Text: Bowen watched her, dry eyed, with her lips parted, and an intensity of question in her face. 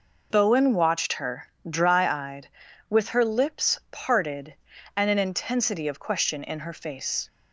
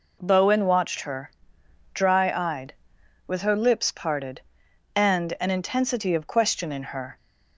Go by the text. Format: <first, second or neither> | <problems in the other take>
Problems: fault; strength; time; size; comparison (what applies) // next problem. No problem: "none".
first | stops before "face"; at 7.1 s